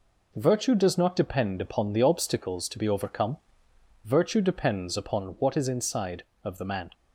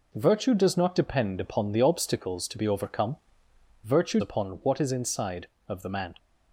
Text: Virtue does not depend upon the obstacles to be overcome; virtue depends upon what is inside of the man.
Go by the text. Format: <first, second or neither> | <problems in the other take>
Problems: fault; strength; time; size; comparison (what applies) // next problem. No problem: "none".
first | skips "depends"; at 4.1 s